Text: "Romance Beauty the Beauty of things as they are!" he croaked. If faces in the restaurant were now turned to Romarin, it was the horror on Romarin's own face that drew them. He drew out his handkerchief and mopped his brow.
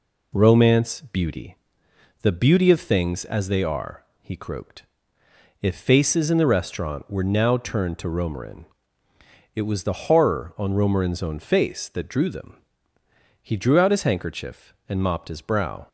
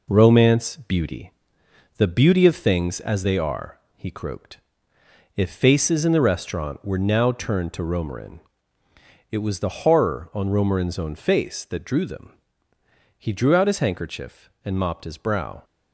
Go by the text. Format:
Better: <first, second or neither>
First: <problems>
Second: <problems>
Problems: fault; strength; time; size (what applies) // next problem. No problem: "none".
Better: first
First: pauses between "Beauty" and "the"; noticeable; at 1.5 s; 0.68 s long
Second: gets quieter; noticeable; throughout; 6 dB // pauses between "Beauty" and "the"; noticeable; at 1.3 s; 0.68 s long